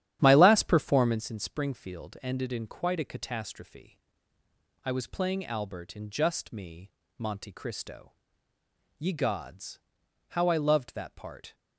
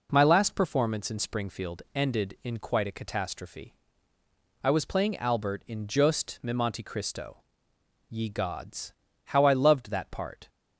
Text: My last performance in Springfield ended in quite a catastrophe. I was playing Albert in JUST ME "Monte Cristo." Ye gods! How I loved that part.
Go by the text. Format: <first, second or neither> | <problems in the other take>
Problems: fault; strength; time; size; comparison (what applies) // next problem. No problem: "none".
second | starts louder than the rest; strong; until 1.2 s; 11 dB // pauses between "ME" and "Monte"; slight; at 6.9 s; 0.26 s long